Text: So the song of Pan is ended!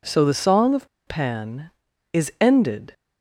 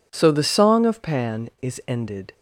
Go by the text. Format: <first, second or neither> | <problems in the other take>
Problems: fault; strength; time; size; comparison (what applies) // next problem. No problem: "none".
second | pauses between "of" and "Pan"; slight; at 0.8 s; 0.20 s long